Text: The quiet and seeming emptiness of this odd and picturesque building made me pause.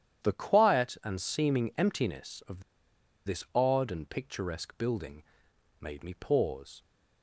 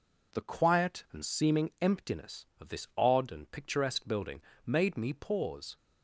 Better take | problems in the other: second | starts louder than the rest; strong; until 1.3 s; 10 dB // pauses between "of" and "this"; noticeable; at 2.6 s; 0.64 s long // pauses between "building" and "made"; noticeable; at 5.2 s; 0.58 s long; slight in the second

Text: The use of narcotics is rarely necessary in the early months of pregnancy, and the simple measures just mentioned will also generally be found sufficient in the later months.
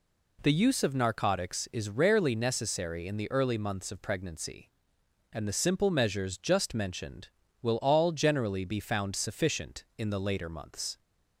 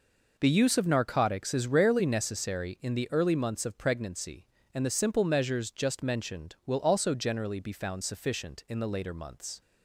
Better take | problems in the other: second | says "all" for "also"; at 7.8 s

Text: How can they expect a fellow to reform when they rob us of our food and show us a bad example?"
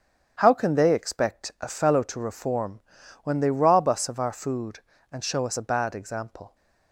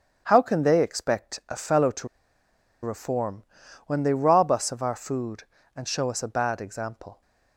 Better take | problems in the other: first | starts louder than the rest; strong; until 1.2 s; 8.5 dB; strong in the first // pauses between "to" and "reform"; noticeable; at 2.0 s; 0.75 s long // pauses between "reform" and "when"; at 3.4 s; 0.42 s long; also in the first

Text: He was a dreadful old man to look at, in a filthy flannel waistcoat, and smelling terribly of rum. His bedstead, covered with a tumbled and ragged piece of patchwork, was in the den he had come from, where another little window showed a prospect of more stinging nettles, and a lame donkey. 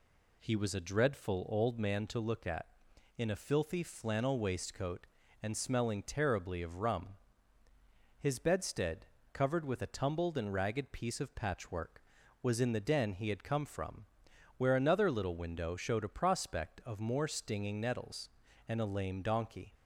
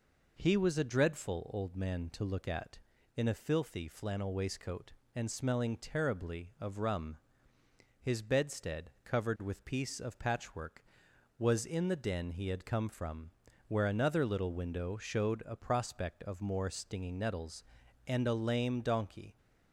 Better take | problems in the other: first | skips "a tumbled and ragged"; at 9.6 s

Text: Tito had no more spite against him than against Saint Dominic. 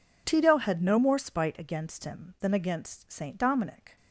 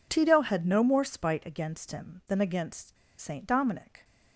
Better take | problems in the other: first | pauses between "against" and "Saint"; slight; at 2.9 s; 0.23 s long

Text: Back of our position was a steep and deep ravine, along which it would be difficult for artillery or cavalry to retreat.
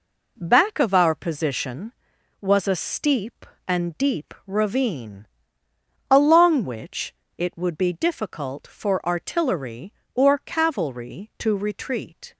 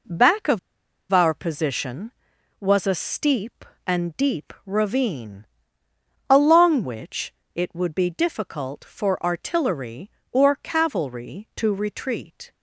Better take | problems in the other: first | pauses between "of" and "our"; noticeable; at 0.5 s; 0.52 s long // pauses between "which" and "it"; slight; at 7.3 s; 0.20 s long; slight in the first

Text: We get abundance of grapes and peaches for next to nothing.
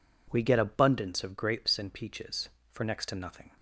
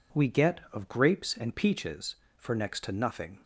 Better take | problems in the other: first | skips "abundance"; at 0.6 s

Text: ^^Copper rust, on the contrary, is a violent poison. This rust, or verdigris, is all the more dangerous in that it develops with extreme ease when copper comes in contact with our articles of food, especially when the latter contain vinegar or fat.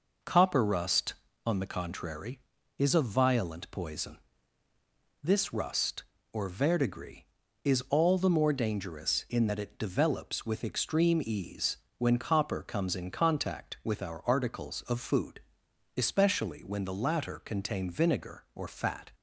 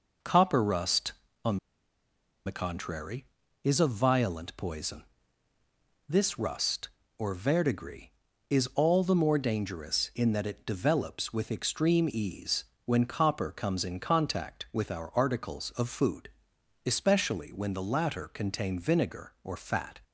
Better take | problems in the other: first | pauses between "on" and "the"; noticeable; at 1.5 s; 0.89 s long // pauses between "ease" and "when"; slight; at 12.6 s; 0.20 s long; slight in the first

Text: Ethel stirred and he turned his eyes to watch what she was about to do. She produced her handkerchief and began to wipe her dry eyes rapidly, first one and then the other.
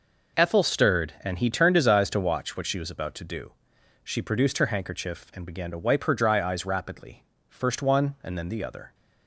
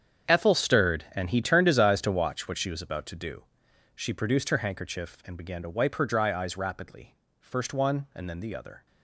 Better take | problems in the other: first | gets quieter; strong; throughout; 14.5 dB

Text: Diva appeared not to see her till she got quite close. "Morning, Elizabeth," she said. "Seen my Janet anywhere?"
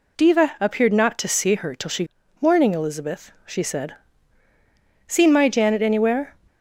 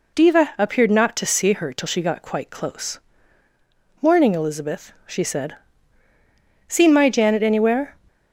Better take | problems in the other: second | skips "got quite close"; at 2.2 s

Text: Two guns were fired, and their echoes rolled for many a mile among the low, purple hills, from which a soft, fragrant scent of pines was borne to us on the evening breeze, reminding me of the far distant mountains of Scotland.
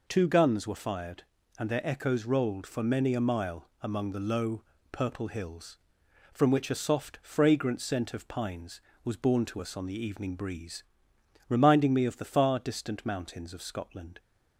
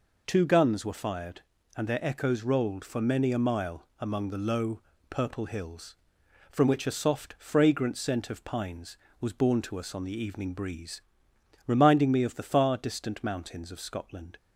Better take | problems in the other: neither | none

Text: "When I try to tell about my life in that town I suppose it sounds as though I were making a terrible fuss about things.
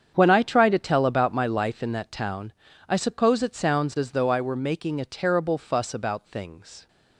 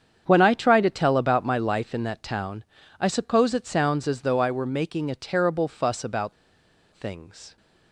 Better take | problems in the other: first | starts louder than the rest; strong; until 1.2 s; 8 dB; strong in the first // pauses between "town" and "I"; slight; at 2.6 s; 0.36 s long; slight in the first // pauses between "about" and "things"; noticeable; at 6.3 s; 0.61 s long

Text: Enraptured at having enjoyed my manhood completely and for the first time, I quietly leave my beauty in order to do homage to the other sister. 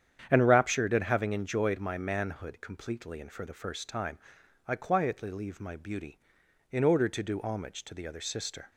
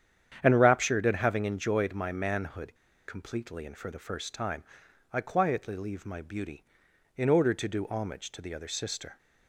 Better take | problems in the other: first | starts louder than the rest; strong; until 1.4 s; 9 dB; strong in the first // pauses between "manhood" and "completely"; slight; at 2.7 s; 0.32 s long

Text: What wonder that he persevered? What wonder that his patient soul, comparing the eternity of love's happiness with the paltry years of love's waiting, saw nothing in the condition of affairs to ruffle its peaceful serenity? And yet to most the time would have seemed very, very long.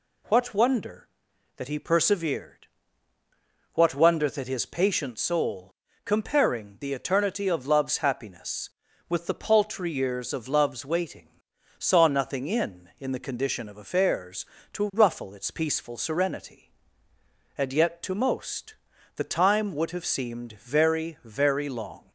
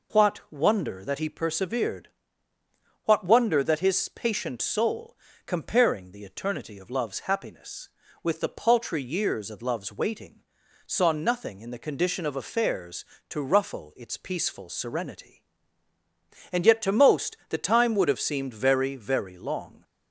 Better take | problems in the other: second | says "in" twice; at 12.9 s // pauses between "most" and "the"; at 18.7 s; 0.42 s long

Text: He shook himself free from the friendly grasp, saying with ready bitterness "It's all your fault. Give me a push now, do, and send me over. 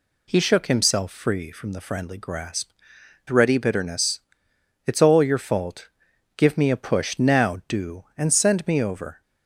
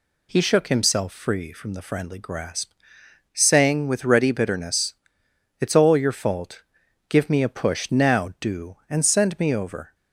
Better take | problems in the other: second | skips "saying with"; at 2.9 s // pauses between "bitterness" and "It's"; noticeable; at 4.2 s; 0.66 s long; noticeable in the second

